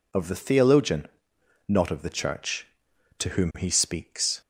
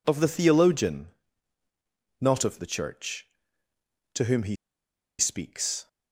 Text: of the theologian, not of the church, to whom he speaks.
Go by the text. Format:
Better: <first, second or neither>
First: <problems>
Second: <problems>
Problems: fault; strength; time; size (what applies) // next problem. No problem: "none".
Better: first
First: none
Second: pauses between "he" and "speaks"; noticeable; at 4.5 s; 0.64 s long